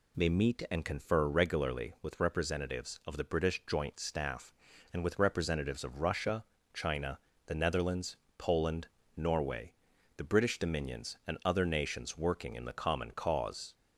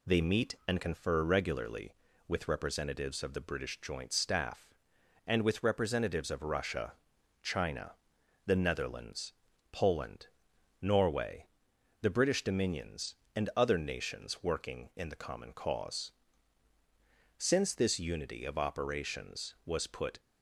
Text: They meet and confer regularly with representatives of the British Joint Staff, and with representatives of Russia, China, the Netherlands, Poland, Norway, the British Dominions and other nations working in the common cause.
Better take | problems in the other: first | goes on to say "Since this unity of operations was put"; strong; from 17.3 s on; 2.8 s long

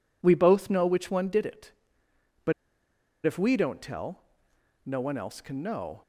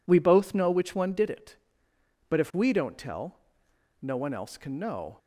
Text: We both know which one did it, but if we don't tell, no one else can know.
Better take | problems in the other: second | pauses between "but" and "if"; noticeable; at 2.5 s; 0.72 s long

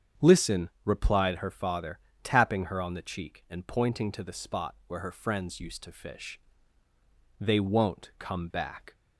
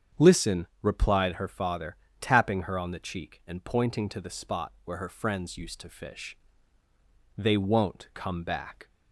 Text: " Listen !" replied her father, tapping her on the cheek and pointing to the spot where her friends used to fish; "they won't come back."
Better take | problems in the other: neither | starts louder than the rest; strong; the same in both

